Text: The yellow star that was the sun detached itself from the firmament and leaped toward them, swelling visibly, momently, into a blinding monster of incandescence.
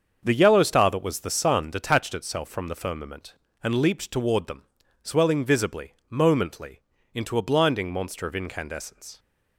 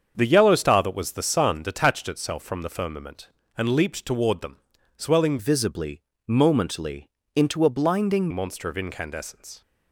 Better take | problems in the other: first | starts louder than the rest; until 1.1 s; 7 dB; also in the first // changes voice from "visibly" to "blinding"; from 5.3 to 8.3 s; 3.0 s long

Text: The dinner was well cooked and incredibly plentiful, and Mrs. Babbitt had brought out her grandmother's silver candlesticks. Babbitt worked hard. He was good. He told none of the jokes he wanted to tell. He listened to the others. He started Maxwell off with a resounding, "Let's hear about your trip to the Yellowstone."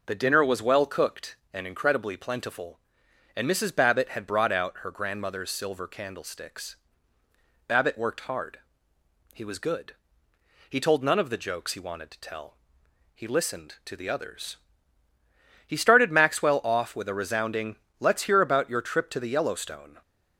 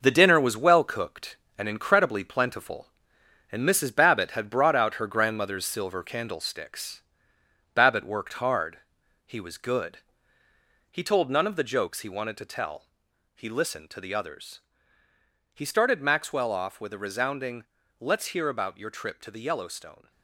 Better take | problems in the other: first | gets quieter; strong; throughout; 8 dB

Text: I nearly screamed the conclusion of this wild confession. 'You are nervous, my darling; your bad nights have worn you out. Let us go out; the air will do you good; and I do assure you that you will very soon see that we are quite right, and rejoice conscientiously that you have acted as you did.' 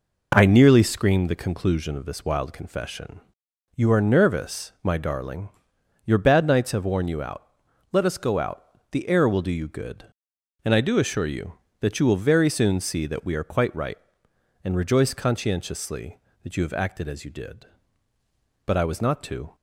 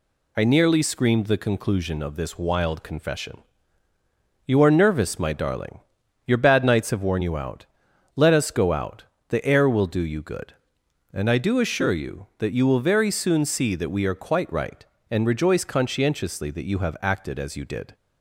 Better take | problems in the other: second | goes on to say "But I was not to"; noticeable; from 18.6 s on; 0.90 s long

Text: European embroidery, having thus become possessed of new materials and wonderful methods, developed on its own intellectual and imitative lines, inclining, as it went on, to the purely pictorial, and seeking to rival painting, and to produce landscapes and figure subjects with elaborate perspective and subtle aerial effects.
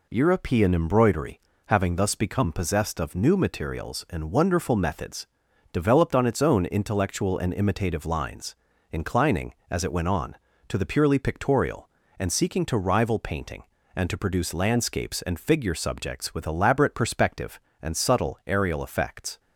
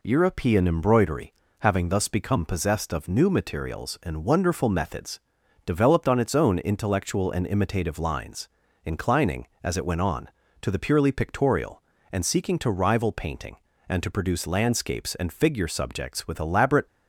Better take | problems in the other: first | stops before "perspective and subtle aerial effects"; at 16.8 s

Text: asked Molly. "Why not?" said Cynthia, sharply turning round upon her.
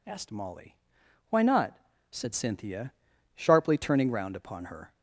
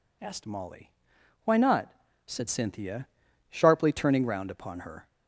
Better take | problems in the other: neither | none

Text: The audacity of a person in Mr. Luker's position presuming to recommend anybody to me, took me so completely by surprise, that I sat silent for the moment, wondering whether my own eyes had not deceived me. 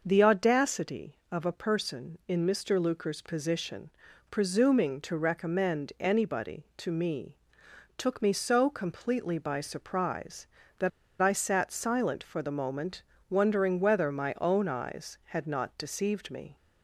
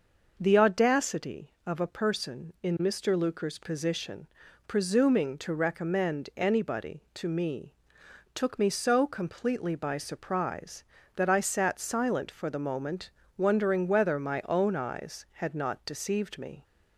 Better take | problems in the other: second | pauses between "position" and "presuming"; at 3.8 s; 0.42 s long; also in the second // pauses between "that" and "I"; slight; at 10.8 s; 0.31 s long

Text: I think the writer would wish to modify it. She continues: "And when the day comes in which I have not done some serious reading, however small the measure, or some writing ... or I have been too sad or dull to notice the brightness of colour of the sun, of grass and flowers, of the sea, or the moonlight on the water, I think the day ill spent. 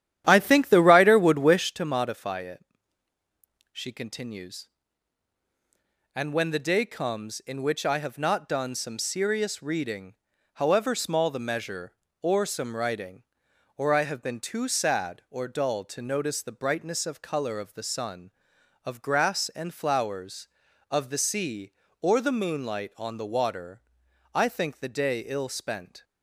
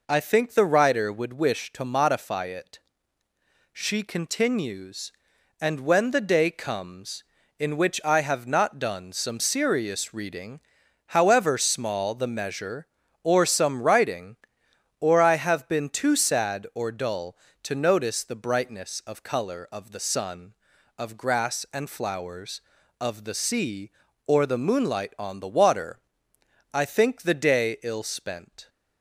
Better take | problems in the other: second | starts louder than the rest; strong; until 1.8 s; 11 dB

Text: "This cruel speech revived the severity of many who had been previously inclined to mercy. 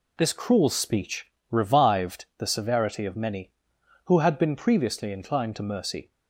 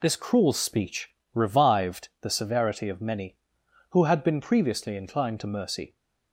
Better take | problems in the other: neither | pauses between "speech" and "revived"; slight; the same in both

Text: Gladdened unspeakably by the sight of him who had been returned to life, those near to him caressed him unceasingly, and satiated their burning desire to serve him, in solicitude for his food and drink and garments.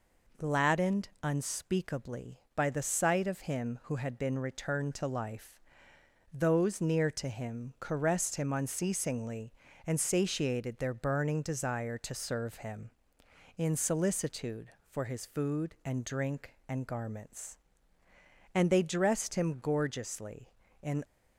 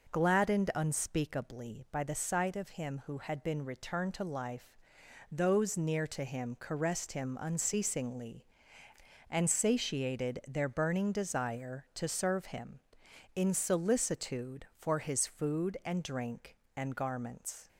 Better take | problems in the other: second | goes on to say "And they dressed him gorgeously in"; strong; from 18.5 s on; 2.5 s long

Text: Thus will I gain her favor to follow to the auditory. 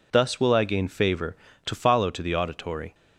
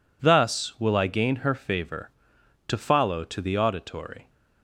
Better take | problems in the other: second | skips "her"; at 0.8 s

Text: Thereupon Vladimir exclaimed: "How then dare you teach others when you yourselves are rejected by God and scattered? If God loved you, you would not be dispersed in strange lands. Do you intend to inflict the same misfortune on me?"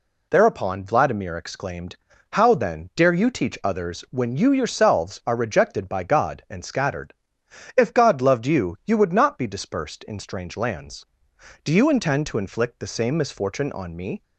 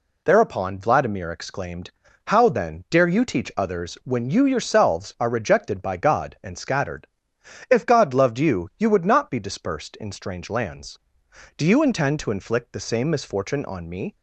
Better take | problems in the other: neither | none

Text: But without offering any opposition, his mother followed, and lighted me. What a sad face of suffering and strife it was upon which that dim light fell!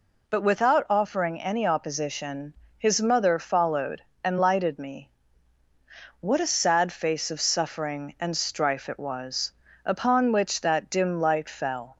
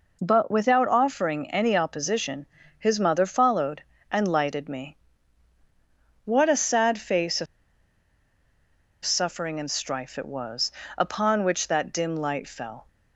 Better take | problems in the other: first | pauses between "of" and "suffering"; strong; at 7.4 s; 1.5 s long // pauses between "was" and "upon"; slight; at 10.7 s; 0.26 s long; slight in the first

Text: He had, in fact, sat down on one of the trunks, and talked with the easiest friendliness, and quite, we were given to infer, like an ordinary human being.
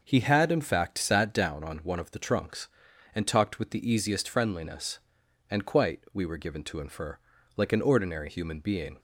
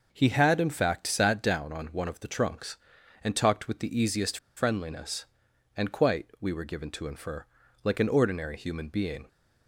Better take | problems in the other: first | pauses between "easiest" and "friendliness"; slight; at 4.3 s; 0.18 s long

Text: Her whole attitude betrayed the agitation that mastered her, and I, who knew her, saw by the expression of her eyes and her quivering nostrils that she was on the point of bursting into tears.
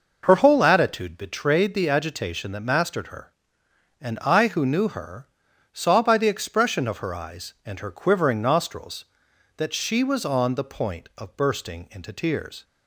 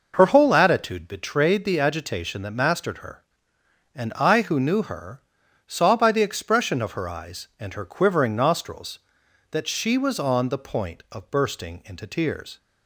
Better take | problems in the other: neither | none

